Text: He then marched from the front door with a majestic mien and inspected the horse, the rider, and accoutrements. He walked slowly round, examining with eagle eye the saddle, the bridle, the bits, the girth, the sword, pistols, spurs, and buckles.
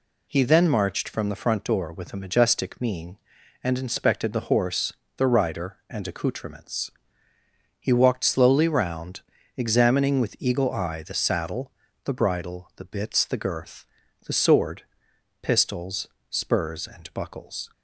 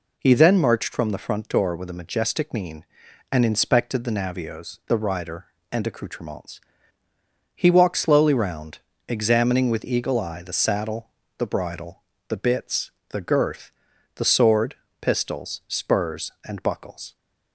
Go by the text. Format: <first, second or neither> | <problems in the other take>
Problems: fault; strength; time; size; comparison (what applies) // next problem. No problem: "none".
first | says "navios" for "horse"; at 4.1 s